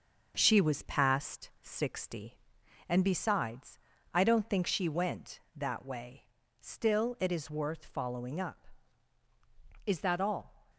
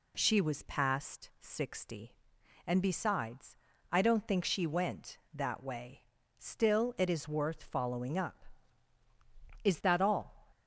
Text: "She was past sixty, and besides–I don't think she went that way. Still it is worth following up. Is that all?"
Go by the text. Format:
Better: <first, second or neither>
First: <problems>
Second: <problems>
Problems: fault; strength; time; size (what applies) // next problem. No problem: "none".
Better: second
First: gets quieter; noticeable; throughout; 5.5 dB // pauses between "past" and "sixty"; slight; at 1.4 s; 0.16 s long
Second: none